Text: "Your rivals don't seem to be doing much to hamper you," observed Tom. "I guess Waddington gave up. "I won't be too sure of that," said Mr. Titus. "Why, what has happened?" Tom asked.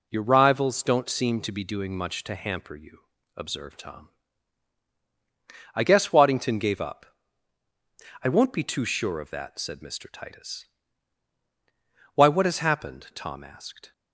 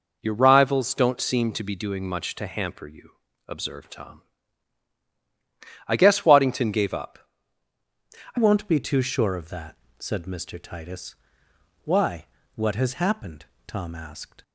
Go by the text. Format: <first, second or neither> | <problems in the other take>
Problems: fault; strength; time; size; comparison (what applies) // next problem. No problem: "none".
first | changes voice at "won't"; from 8.3 s on; 6.1 s long